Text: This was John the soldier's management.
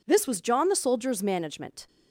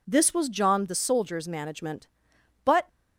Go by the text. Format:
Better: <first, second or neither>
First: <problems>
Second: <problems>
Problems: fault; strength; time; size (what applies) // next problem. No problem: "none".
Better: first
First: none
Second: goes on to say "But"; slight; from 2.6 s on; 0.24 s long